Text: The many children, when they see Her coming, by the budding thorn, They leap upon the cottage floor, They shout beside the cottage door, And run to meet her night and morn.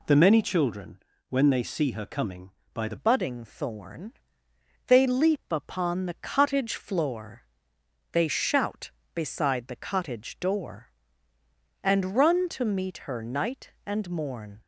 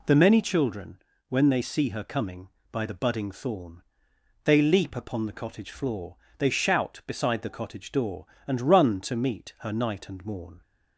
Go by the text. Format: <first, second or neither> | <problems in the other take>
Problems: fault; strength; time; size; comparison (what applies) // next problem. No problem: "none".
second | changes voice at "budding"; from 2.9 s on; 11.7 s long